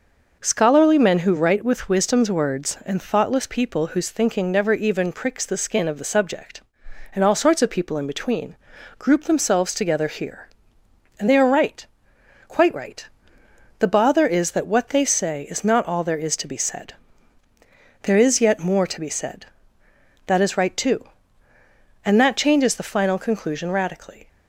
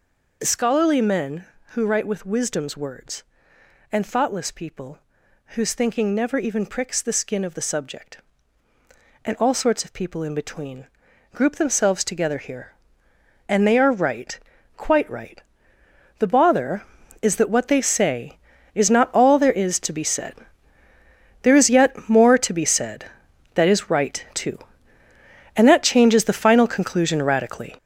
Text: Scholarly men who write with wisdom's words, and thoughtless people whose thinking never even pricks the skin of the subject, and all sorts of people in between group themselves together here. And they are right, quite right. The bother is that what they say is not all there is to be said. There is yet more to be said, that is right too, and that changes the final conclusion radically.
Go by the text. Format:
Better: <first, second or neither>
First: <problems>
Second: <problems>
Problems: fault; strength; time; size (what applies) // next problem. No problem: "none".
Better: first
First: pauses between "between" and "group"; at 8.5 s; 0.44 s long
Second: gets louder; strong; throughout; 8.5 dB // pauses between "people" and "whose"; noticeable; at 4.9 s; 0.56 s long // pauses between "between" and "group"; at 10.8 s; 0.44 s long